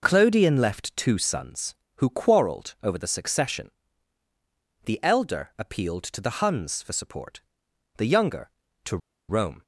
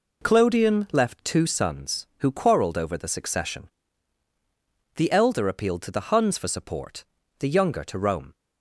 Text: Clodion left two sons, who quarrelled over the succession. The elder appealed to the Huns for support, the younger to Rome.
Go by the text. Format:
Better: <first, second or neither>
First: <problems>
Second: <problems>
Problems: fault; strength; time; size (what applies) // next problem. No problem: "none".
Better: second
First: pauses between "to" and "Rome"; slight; at 8.9 s; 0.31 s long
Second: none